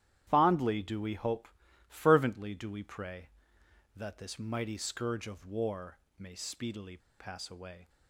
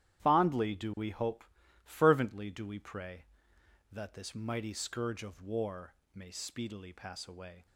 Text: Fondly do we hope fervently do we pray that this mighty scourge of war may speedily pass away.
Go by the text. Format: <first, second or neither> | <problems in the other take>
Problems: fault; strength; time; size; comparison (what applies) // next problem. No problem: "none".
second | starts louder than the rest; strong; until 1.2 s; 11.5 dB; strong in the second // pauses between "hope" and "fervently"; at 1.4 s; 0.40 s long; also in the second // pauses between "war" and "may"; slight; at 5.9 s; 0.22 s long; slight in the second // pauses between "speedily" and "pass"; slight; at 6.9 s; 0.21 s long